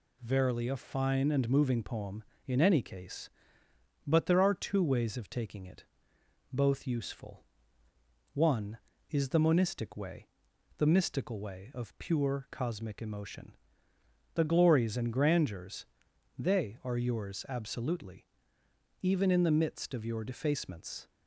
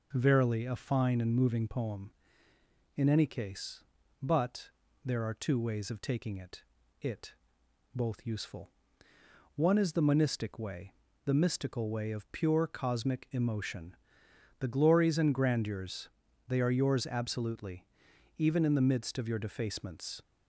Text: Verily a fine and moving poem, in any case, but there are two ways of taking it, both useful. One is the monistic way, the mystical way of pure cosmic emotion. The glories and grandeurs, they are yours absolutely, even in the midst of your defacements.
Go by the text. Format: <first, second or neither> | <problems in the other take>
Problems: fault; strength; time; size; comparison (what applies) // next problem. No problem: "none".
first | pauses between "but" and "there"; at 4.6 s; 0.38 s long // says "it" twice; at 7.0 s